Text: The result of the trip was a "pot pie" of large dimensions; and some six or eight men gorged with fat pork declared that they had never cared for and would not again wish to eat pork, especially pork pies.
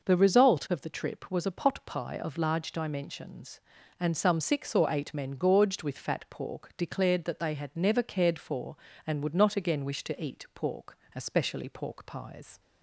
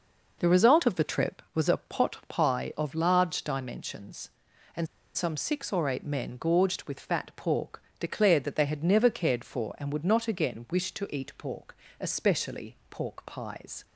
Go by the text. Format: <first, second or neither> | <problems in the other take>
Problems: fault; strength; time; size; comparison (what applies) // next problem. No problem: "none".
first | pauses between "and" and "some"; slight; at 4.8 s; 0.28 s long // pauses between "pork" and "declared"; slight; at 7.8 s; 0.18 s long